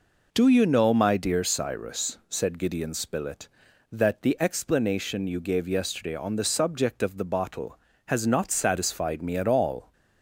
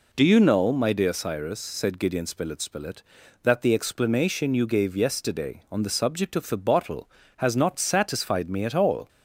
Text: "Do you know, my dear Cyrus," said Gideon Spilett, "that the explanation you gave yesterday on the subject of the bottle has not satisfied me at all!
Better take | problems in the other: first | says "Spilett" twice; at 2.5 s

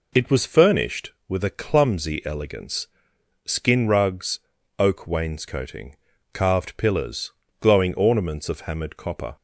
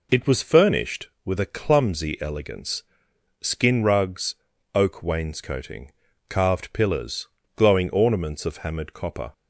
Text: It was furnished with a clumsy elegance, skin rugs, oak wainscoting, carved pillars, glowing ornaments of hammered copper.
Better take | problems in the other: neither | none

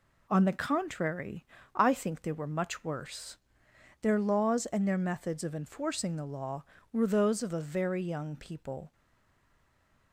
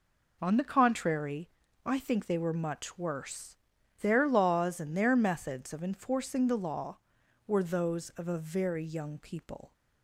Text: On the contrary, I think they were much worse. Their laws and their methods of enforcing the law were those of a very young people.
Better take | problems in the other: second | stays silent after the last word; noticeable; from 8.9 s on; 1.2 s long

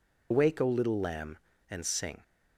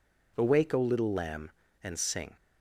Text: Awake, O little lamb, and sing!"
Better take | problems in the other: second | loses the start of "Awake"; at 0.3 s; 80 ms

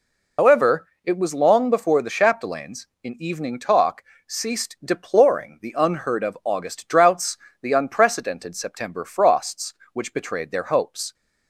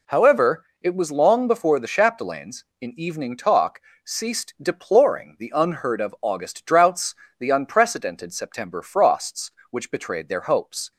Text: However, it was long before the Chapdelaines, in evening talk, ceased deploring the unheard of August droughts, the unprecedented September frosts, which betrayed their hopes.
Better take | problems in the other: second | loses the start of "However"; at 0.3 s; 90 ms

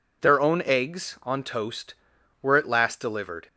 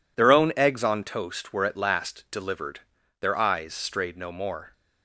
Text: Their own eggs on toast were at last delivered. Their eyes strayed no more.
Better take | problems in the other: second | stops before "Their eyes strayed no more"; at 3.4 s

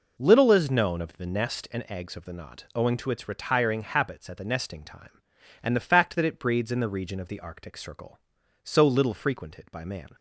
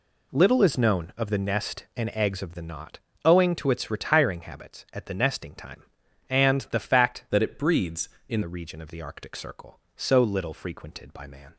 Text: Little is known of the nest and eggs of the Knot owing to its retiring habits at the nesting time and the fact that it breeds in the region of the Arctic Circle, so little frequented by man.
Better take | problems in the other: first | pauses between "Knot" and "owing"; slight; at 2.9 s; 0.26 s long // changes voice from "that" to "in"; from 7.2 to 8.4 s; 1.2 s long

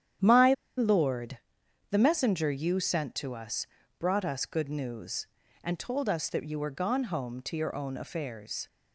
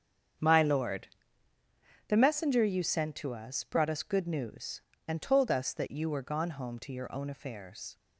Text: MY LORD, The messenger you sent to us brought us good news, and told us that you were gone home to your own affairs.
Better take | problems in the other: second | starts louder than the rest; strong; until 2.0 s; 10 dB; strong in the second // pauses between "MY" and "LORD"; slight; at 0.5 s; 0.24 s long // pauses between "us" and "brought"; slight; at 3.6 s; 0.32 s long

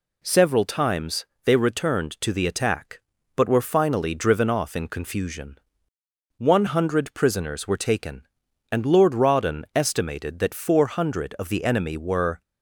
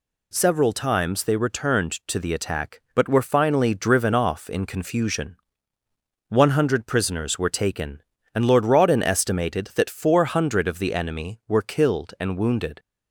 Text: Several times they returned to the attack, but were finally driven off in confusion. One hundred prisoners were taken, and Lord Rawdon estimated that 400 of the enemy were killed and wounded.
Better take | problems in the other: second | pauses between "times" and "they"; slight; at 1.2 s; 0.18 s long // stops before "killed and wounded"; at 12.4 s

